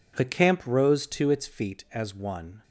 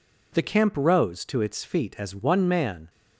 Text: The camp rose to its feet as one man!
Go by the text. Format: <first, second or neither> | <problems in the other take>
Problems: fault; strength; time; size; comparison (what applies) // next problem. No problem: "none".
second | stops before "man"; at 2.6 s